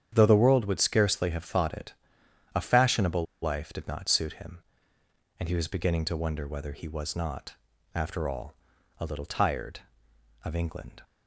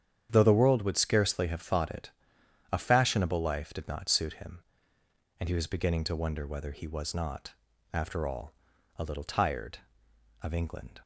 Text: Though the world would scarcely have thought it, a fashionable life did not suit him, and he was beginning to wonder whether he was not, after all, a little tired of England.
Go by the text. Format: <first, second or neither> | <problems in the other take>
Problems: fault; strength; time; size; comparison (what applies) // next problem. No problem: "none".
second | starts louder than the rest; strong; until 1.1 s; 8.5 dB; strong in the second // pauses between "fashionable" and "life"; slight; at 3.2 s; 0.18 s long